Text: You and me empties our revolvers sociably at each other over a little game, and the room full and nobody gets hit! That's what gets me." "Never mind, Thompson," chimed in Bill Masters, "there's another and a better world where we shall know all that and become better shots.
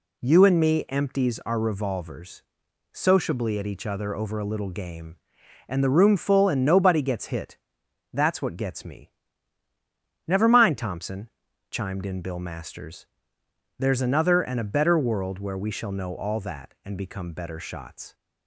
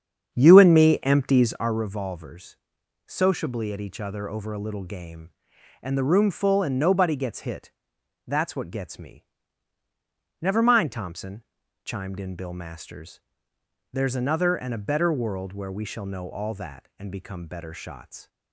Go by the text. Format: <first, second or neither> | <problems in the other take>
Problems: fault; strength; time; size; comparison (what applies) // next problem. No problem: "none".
first | starts louder than the rest; strong; until 1.8 s; 8 dB // pauses between "revolvers" and "sociably"; noticeable; at 2.5 s; 0.48 s long; noticeable in the first